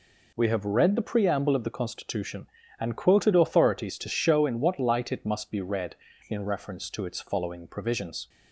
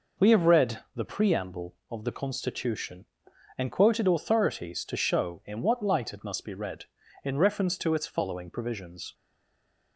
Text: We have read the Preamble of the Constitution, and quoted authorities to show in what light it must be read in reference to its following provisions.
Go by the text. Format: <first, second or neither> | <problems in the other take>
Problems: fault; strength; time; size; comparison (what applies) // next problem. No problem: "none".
first | pauses between "read" and "the"; slight; at 0.7 s; 0.16 s long // stays silent after the last word; slight; from 9.1 s on; 0.8 s long